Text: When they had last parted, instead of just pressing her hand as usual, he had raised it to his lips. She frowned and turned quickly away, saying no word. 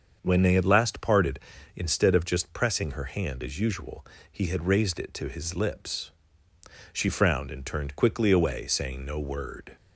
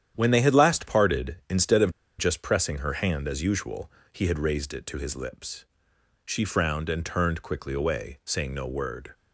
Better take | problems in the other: first | starts louder than the rest; strong; until 1.1 s; 10 dB; also in the first // pauses between "of" and "just"; slight; at 1.8 s; 0.28 s long

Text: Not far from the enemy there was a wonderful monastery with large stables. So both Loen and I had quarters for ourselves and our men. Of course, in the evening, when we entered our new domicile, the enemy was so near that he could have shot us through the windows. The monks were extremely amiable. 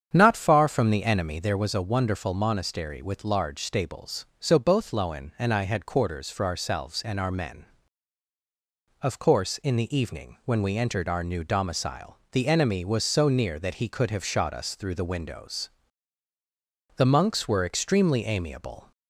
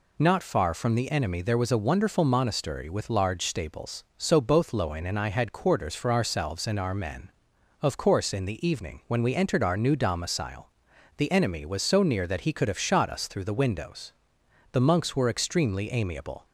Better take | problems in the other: second | starts louder than the rest; strong; until 1.3 s; 8 dB

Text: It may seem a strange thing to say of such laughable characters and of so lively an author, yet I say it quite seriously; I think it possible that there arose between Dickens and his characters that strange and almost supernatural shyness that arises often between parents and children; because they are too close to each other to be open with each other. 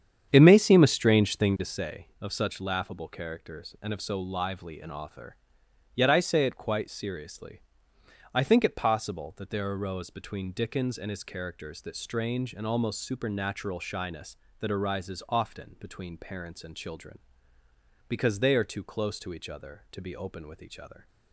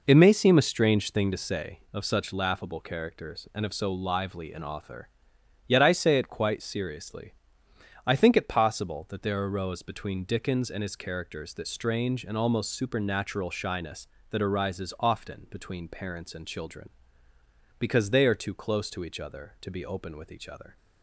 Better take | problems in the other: second | starts louder than the rest; strong; until 1.8 s; 8.5 dB

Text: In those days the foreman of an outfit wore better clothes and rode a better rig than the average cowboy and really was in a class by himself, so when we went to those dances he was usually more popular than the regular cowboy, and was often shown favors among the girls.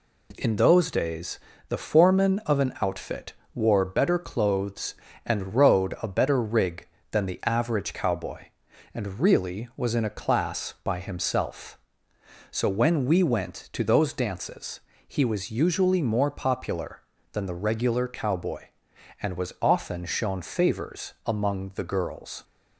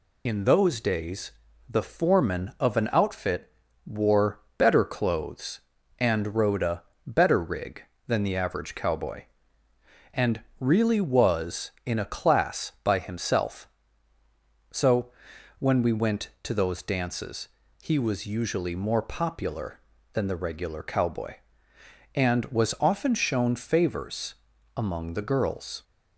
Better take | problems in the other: first | loses the start of "In"; at 0.2 s; 40 ms // pauses between "days" and "the"; at 1.3 s; 0.38 s long; slight in the first // pauses between "outfit" and "wore"; slight; at 3.5 s; 0.34 s long; slight in the first // pauses between "wore" and "better"; slight; at 4.3 s; 0.18 s long // pauses between "a" and "better"; slight; at 6.8 s; 0.22 s long // pauses between "and" and "really"; slight; at 10.4 s; 0.18 s long // pauses between "so" and "when"; noticeable; at 15.0 s; 0.50 s long // pauses between "dances" and "he"; slight; at 17.4 s; 0.34 s long; slight in the first // pauses between "favors" and "among"; at 24.3 s; 0.42 s long

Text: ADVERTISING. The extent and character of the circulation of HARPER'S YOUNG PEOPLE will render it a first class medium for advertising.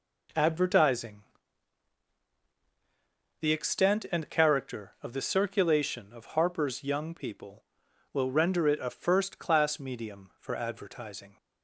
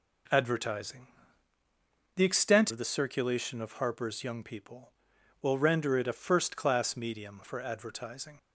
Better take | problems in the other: first | skips "and character"; at 2.7 s

